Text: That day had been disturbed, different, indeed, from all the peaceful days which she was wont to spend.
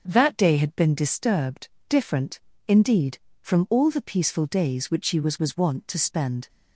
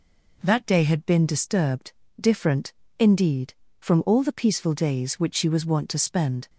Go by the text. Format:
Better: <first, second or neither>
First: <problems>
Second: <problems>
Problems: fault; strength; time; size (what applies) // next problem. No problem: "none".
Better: second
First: starts louder than the rest; until 1.0 s; 7 dB // says "was" twice; at 5.3 s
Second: none